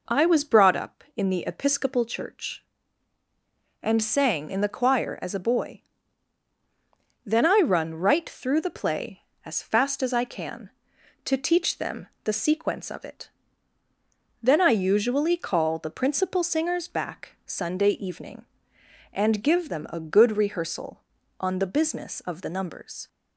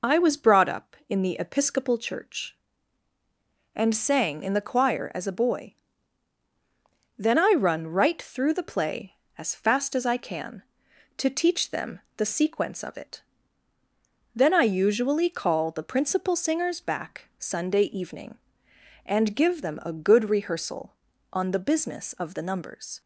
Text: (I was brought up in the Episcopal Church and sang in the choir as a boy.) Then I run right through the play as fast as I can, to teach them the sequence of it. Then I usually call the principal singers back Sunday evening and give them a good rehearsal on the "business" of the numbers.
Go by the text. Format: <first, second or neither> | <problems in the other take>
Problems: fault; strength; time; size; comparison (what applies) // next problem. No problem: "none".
first | loses the start of "I"; at 0.0 s; 30 ms // pauses between "them" and "the"; slight; at 11.9 s; 0.18 s long; slight in the first